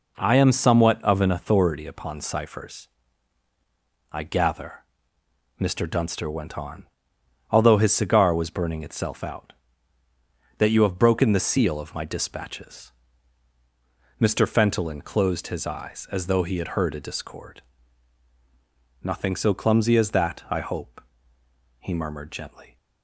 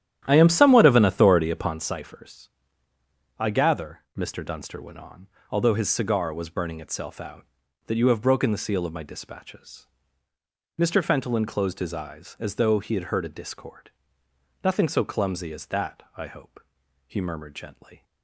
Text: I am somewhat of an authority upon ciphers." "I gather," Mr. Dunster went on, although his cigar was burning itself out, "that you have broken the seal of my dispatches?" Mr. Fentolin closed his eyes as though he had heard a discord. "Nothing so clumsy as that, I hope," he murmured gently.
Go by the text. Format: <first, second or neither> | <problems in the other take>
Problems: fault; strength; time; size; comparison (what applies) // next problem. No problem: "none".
first | starts louder than the rest; strong; until 1.8 s; 11 dB